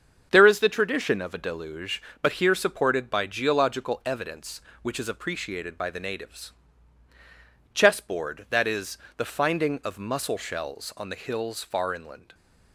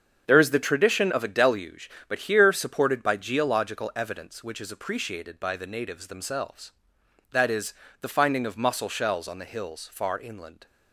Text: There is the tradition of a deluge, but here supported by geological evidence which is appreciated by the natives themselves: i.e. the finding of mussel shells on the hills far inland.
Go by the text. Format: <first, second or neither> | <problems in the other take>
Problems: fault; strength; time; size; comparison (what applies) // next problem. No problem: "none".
second | starts louder than the rest; strong; until 1.3 s; 7.5 dB; strong in the second // says "chessboard" for "themselves"; at 7.7 s